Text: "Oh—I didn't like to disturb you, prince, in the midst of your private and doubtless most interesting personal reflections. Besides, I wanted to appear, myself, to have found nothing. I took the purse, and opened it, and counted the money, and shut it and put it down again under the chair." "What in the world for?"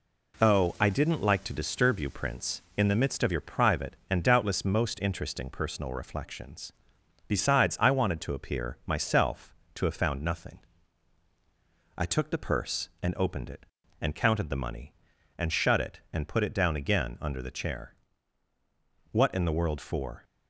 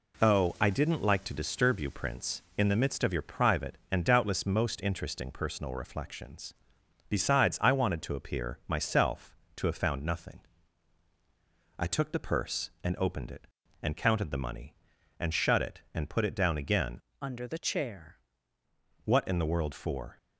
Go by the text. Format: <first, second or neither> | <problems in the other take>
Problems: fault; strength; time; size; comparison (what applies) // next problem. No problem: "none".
first | changes voice from "under" to "chair"; from 17.2 to 18.1 s; 0.9 s long